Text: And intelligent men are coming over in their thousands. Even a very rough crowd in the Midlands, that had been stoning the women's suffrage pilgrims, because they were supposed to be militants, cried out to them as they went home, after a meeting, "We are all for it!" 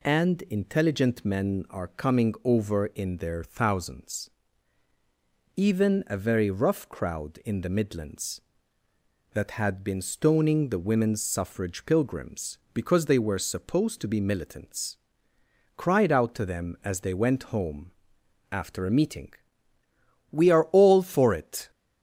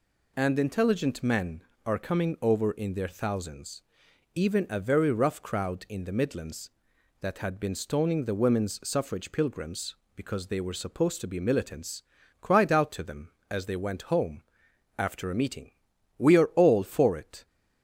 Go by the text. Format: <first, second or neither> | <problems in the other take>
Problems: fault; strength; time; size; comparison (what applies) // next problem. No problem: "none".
neither | none